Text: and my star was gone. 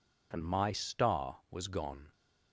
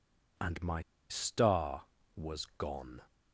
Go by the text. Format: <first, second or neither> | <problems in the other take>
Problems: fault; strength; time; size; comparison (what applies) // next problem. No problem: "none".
first | pauses between "my" and "star"; slight; at 0.8 s; 0.28 s long